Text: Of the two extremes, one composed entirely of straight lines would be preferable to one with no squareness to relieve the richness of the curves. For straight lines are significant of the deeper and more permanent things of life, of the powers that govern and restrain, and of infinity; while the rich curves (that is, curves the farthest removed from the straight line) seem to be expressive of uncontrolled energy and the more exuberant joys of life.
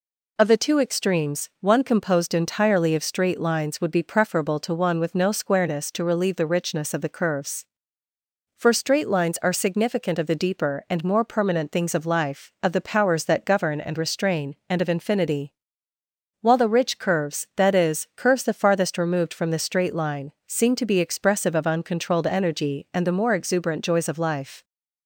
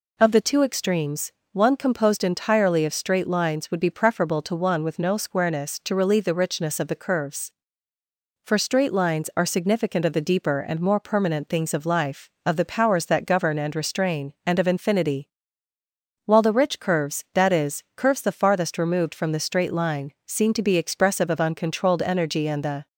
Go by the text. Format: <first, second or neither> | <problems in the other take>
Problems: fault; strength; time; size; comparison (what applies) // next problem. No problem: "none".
first | stops before "more exuberant joys of life"; at 22.8 s